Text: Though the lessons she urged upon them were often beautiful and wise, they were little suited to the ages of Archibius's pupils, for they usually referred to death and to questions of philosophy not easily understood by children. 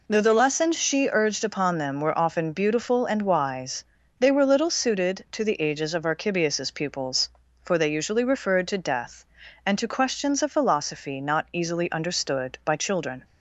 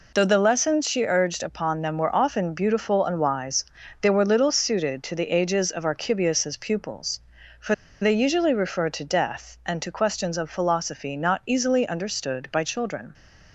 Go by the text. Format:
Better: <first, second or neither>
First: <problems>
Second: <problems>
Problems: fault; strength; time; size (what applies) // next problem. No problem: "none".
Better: first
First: none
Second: pauses between "for" and "they"; slight; at 7.7 s; 0.26 s long